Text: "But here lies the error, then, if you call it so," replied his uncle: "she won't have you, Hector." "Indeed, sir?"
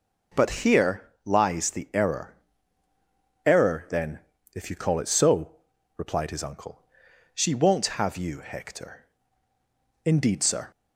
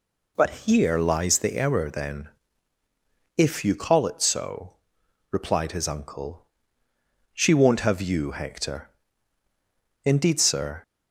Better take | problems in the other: second | pauses between "here" and "lies"; slight; at 1.0 s; 0.22 s long // says "error" twice; at 3.4 s

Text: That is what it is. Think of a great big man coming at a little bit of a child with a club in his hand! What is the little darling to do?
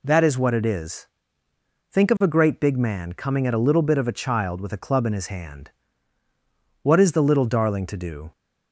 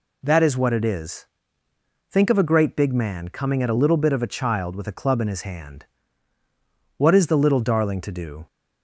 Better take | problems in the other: neither | none

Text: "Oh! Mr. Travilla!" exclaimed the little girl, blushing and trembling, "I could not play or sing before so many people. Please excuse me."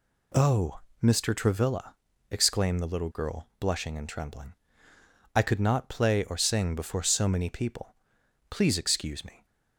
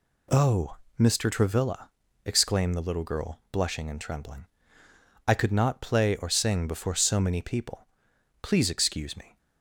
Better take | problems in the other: neither | none

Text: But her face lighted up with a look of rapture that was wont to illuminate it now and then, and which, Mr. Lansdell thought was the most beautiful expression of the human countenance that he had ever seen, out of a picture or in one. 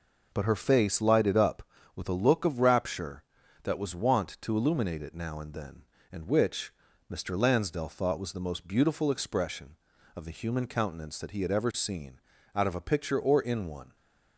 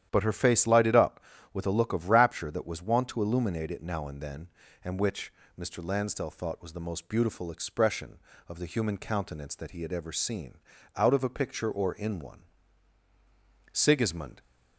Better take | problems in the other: first | starts louder than the rest; strong; until 1.1 s; 10.5 dB // goes on to say "Sigismund"; noticeable; from 13.7 s on; 0.68 s long

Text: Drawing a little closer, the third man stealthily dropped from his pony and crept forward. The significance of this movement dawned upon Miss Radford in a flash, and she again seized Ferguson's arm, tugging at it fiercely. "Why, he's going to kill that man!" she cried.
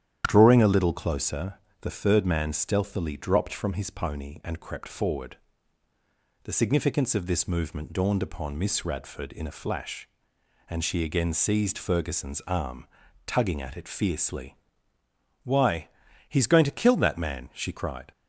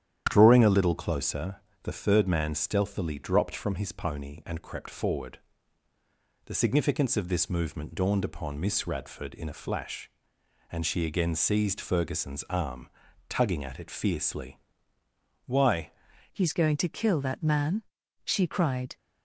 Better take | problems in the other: first | starts louder than the rest; strong; until 1.3 s; 10 dB; strong in the first // changes voice at "he's"; from 16.3 s on; 2.6 s long

